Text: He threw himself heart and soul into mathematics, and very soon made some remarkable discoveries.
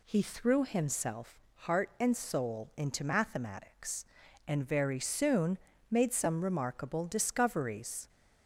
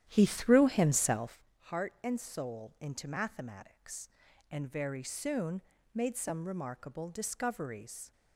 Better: first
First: pauses between "himself" and "heart"; slight; at 1.3 s; 0.16 s long // pauses between "soon" and "made"; slight; at 5.5 s; 0.32 s long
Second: starts louder than the rest; strong; until 1.4 s; 11 dB // pauses between "himself" and "heart"; slight; at 1.4 s; 0.16 s long // pauses between "soon" and "made"; slight; at 5.6 s; 0.32 s long

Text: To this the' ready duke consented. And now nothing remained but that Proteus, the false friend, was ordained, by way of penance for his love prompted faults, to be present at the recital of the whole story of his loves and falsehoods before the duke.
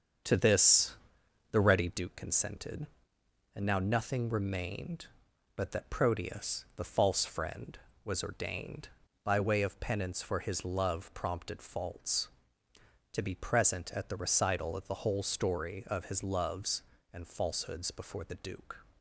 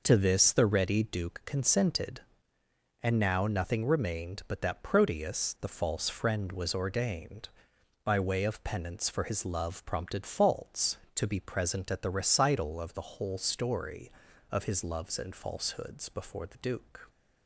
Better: second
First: starts louder than the rest; strong; until 1.9 s; 7.5 dB // pauses between "this" and "the"; noticeable; at 0.9 s; 0.56 s long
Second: none

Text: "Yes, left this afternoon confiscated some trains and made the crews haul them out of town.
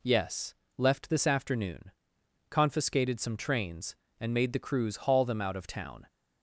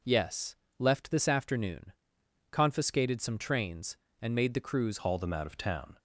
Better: first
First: pauses between "afternoon" and "confiscated"; noticeable; at 1.9 s; 0.58 s long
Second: pauses between "afternoon" and "confiscated"; noticeable; at 1.9 s; 0.58 s long // changes voice at "haul"; from 4.9 s on; 1.0 s long

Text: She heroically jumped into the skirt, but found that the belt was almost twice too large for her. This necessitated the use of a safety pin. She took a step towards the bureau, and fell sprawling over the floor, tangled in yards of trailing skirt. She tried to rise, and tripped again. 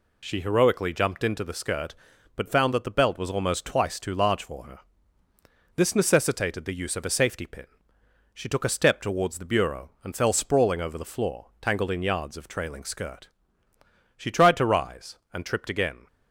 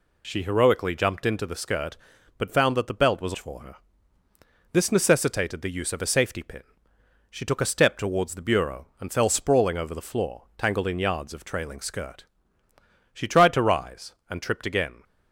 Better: first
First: none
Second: skips "almost twice too large"; at 3.3 s

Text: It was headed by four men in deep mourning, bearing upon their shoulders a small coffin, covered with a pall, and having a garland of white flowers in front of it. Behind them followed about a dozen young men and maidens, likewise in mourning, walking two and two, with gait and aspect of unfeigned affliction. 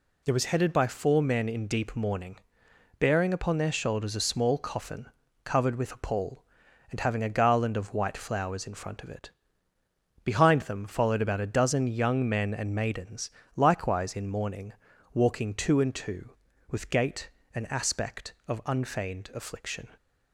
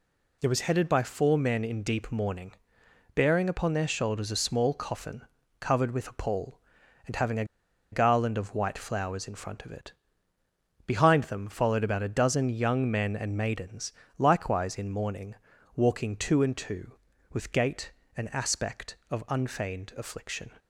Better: first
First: none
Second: pauses between "a" and "garland"; noticeable; at 7.4 s; 0.47 s long

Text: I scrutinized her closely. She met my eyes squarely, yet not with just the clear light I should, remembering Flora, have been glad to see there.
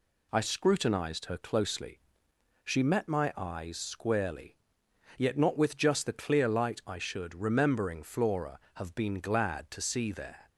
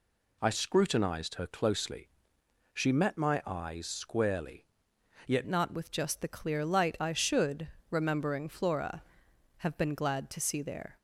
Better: first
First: none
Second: changes voice at "not"; from 5.4 s on; 5.5 s long

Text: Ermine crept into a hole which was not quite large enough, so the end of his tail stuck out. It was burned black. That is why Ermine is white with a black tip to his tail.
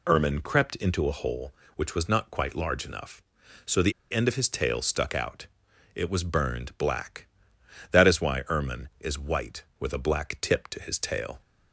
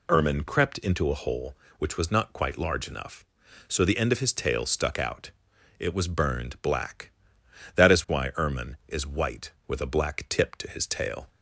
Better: second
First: pauses between "the" and "end"; slight; at 3.9 s; 0.19 s long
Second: none

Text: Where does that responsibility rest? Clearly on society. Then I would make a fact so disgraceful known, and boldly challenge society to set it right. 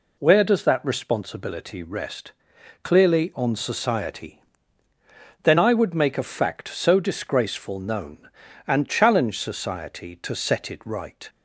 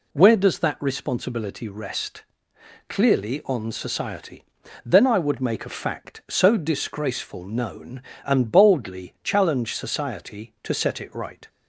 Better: second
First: skips "boldly"; at 8.8 s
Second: none

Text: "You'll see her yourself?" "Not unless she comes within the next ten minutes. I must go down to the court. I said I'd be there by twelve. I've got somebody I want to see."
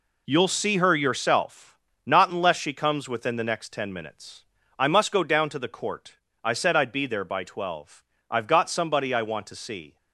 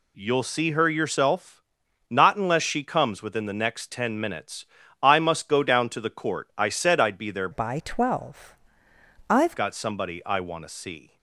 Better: first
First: none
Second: changes voice from "by" to "I've"; from 7.5 to 9.5 s; 2.0 s long

